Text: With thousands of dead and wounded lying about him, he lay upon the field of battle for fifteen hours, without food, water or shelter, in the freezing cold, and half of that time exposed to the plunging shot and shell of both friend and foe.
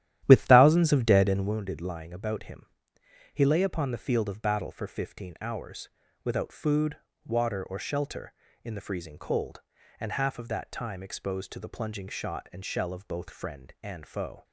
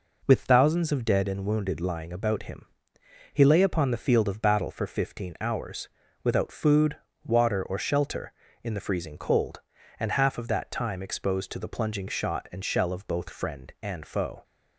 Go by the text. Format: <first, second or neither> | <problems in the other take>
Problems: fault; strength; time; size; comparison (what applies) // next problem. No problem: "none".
second | starts louder than the rest; strong; until 1.5 s; 12 dB